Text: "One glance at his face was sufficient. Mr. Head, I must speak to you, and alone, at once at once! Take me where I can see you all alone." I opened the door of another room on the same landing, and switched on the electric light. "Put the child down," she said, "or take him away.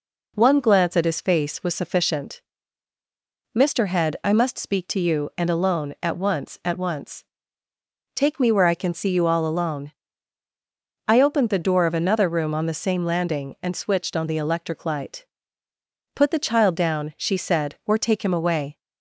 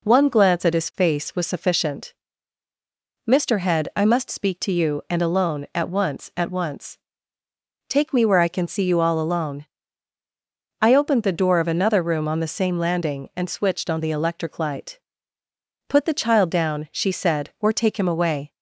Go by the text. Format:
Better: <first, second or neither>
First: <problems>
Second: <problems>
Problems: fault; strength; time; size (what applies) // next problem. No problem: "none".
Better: neither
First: none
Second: none